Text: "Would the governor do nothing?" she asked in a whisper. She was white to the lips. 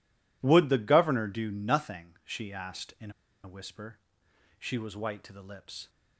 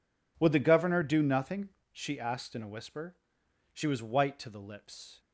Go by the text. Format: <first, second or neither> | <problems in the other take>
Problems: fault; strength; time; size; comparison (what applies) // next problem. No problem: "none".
second | pauses between "in" and "a"; slight; at 3.0 s; 0.33 s long